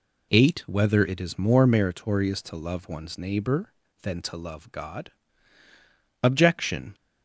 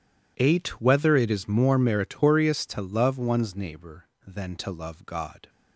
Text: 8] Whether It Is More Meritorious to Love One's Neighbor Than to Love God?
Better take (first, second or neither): second